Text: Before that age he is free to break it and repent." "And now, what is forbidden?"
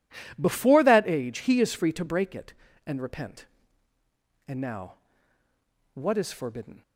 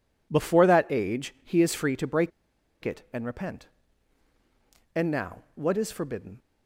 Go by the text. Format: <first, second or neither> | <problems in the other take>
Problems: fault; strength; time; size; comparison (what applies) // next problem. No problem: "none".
first | pauses between "break" and "it"; noticeable; at 2.3 s; 0.53 s long